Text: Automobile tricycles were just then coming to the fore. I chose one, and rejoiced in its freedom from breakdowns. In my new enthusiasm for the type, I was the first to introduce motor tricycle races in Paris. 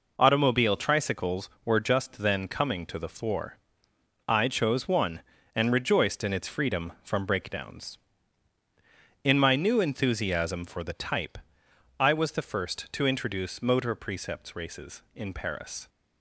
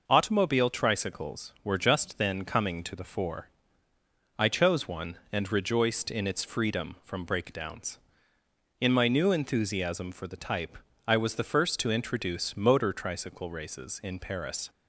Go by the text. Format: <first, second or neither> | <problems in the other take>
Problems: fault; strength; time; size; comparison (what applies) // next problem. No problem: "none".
second | says "precepts" for "tricycle"; at 13.9 s